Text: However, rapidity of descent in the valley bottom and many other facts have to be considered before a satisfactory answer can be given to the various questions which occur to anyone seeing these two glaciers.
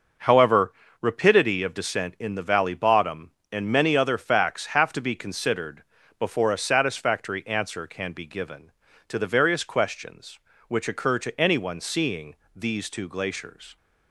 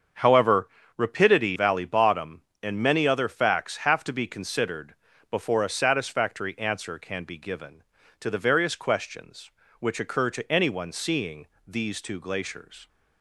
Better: first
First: starts louder than the rest; noticeable; until 1.4 s; 6 dB // pauses between "considered" and "before"; slight; at 5.8 s; 0.36 s long // pauses between "seeing" and "these"; slight; at 12.3 s; 0.20 s long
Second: starts louder than the rest; until 1.4 s; 7 dB // skips "of descent in the"; at 1.5 s // pauses between "considered" and "before"; slight; at 4.9 s; 0.36 s long // pauses between "seeing" and "these"; slight; at 11.4 s; 0.20 s long

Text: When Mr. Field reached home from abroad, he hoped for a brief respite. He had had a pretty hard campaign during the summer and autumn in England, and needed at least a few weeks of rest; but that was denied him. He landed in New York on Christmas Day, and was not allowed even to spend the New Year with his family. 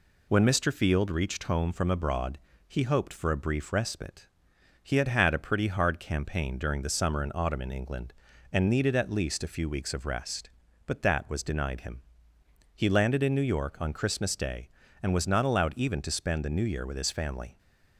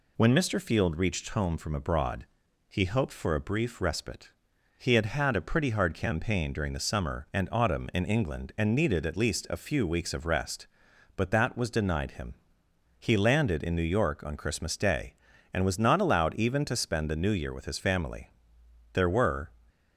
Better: first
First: none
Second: goes on to say "There were"; from 18.9 s on; 0.56 s long

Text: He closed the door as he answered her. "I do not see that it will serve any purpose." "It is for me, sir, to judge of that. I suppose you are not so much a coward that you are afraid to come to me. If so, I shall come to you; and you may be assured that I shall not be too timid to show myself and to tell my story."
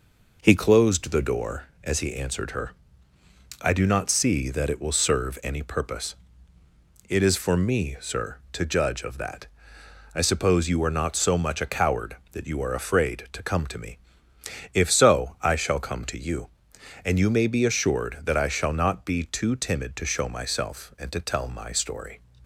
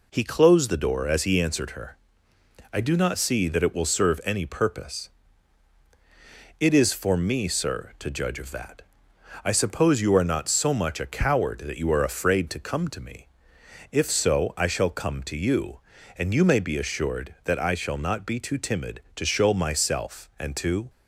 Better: first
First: none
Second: stops before "tell my story"; at 20.8 s

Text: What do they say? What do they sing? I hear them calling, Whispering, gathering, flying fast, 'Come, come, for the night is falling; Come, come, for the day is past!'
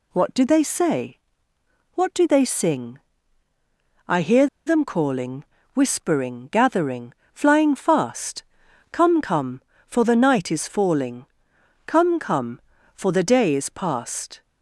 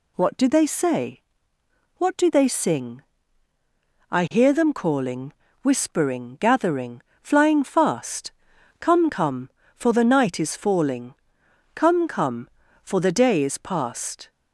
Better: second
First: pauses between "hear" and "them"; slight; at 4.4 s; 0.20 s long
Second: none

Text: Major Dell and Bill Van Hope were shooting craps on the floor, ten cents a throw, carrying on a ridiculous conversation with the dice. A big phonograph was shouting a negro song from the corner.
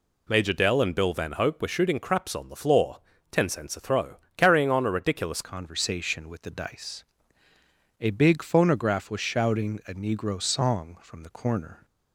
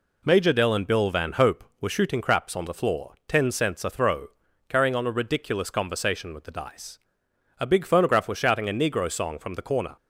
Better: second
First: changes voice at "conversation"; from 5.4 s on; 6.4 s long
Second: none

